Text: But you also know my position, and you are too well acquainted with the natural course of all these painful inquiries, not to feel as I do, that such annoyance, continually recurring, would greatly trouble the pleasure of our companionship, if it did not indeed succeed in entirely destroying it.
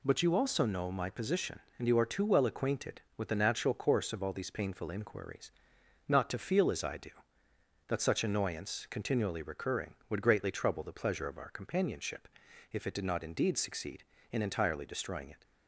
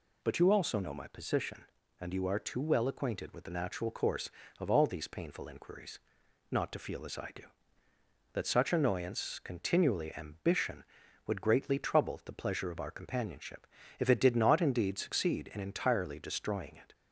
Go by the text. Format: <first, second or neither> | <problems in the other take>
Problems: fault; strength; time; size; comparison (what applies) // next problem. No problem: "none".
first | says "ambition" for "recurring"; at 10.1 s